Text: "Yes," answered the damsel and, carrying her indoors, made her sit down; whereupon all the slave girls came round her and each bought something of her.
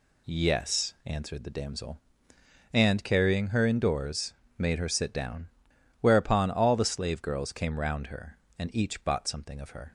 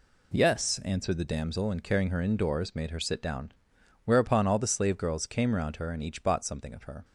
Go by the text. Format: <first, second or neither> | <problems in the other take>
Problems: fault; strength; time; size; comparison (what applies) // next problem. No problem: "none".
neither | none